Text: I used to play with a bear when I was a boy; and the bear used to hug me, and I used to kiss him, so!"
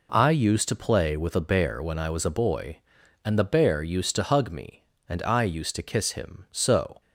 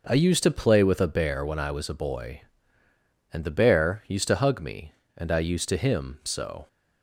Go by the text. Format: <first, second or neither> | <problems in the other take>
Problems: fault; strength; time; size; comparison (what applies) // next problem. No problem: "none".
first | skips "kiss"; at 5.7 s